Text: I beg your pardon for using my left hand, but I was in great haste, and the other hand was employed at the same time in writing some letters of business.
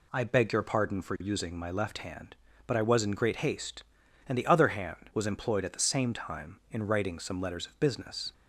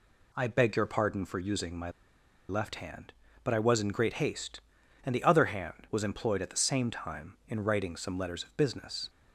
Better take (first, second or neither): first